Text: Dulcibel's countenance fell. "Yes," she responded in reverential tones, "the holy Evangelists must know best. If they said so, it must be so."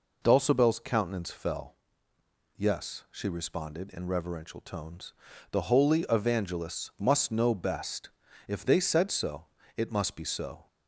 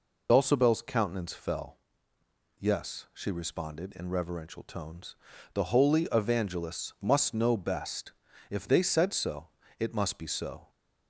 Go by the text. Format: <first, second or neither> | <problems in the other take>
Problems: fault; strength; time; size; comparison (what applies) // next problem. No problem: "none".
first | loses the start of "Dulcibel's"; at 0.2 s; 45 ms